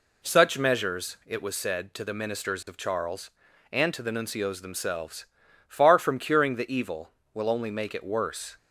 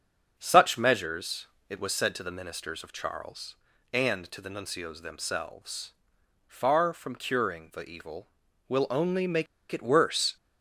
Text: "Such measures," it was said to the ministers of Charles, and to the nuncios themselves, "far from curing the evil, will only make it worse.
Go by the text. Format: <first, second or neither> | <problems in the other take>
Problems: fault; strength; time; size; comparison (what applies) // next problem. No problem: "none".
first | starts louder than the rest; until 1.3 s; 7 dB // pauses between "make" and "it"; slight; at 9.4 s; 0.25 s long